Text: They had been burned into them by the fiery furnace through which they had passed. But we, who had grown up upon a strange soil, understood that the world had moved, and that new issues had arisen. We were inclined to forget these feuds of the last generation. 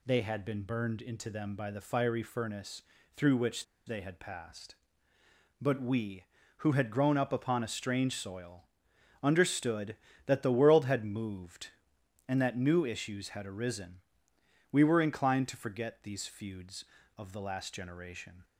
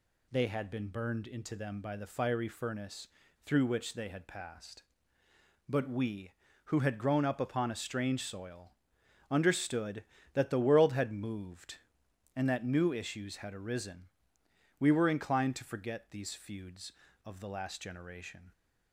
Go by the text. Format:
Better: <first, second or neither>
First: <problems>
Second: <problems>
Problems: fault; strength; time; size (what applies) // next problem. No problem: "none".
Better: second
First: pauses between "furnace" and "through"; slight; at 2.8 s; 0.32 s long // pauses between "which" and "they"; slight; at 3.6 s; 0.22 s long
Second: pauses between "furnace" and "through"; slight; at 3.0 s; 0.35 s long